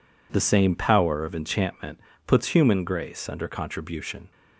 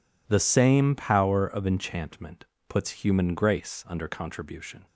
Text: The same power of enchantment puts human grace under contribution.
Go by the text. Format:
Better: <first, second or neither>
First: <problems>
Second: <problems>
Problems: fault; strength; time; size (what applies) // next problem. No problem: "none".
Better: neither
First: pauses between "enchantment" and "puts"; slight; at 1.9 s; 0.26 s long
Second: pauses between "enchantment" and "puts"; slight; at 2.4 s; 0.22 s long